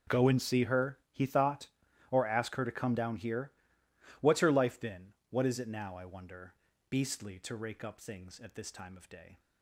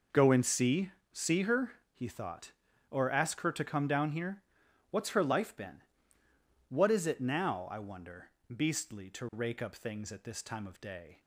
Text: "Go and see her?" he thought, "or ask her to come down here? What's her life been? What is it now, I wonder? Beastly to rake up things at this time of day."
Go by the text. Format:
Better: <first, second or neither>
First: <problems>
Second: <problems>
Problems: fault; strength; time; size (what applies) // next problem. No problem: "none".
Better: first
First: none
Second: says "see" twice; at 1.1 s